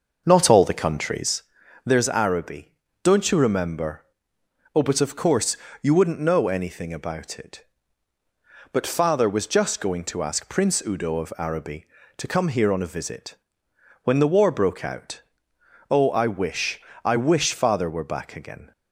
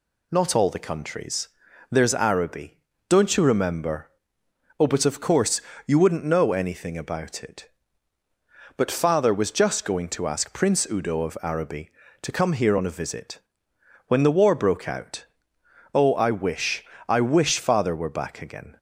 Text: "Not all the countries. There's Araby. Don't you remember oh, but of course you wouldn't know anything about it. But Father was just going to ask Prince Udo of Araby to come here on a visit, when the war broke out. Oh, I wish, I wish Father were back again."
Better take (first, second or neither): second